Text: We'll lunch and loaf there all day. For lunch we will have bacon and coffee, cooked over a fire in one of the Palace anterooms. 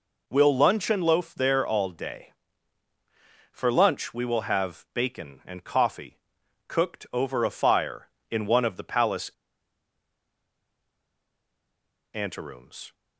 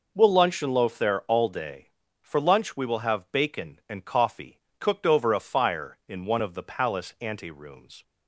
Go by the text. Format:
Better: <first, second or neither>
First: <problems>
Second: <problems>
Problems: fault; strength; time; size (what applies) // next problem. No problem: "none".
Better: second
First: pauses between "Palace" and "anterooms"; strong; at 9.2 s; 2.8 s long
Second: none